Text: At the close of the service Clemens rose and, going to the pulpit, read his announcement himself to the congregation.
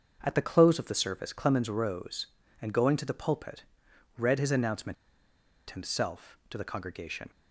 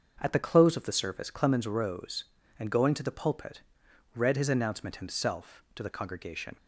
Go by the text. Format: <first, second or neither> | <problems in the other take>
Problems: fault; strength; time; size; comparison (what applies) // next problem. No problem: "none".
second | starts louder than the rest; until 1.2 s; 6.5 dB; also in the second // pauses between "announcement" and "himself"; noticeable; at 4.9 s; 0.75 s long